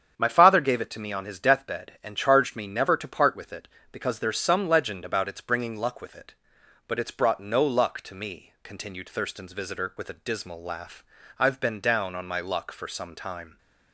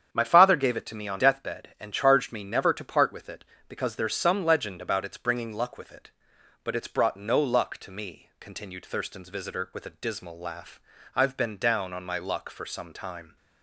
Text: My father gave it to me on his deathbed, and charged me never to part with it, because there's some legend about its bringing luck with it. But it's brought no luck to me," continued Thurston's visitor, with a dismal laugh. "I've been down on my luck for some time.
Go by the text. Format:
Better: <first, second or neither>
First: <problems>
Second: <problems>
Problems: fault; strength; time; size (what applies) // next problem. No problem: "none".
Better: first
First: starts louder than the rest; strong; until 1.2 s; 8 dB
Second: starts louder than the rest; strong; until 1.1 s; 8 dB // skips "his"; at 1.1 s